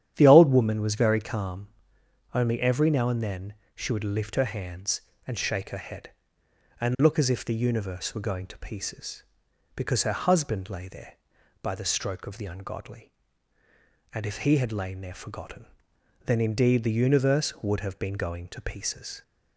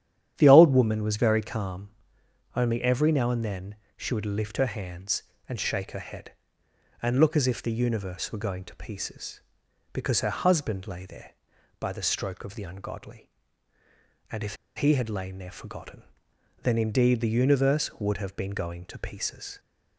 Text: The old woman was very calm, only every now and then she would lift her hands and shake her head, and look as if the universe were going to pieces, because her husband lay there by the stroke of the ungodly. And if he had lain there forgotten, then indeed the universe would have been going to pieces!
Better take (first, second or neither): first